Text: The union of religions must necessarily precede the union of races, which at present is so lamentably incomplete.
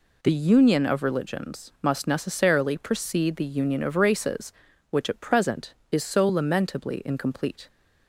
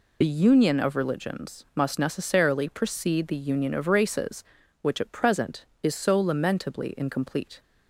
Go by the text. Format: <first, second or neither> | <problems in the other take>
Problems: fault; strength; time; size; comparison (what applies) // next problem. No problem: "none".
first | loses the start of "The"; at 0.2 s; 40 ms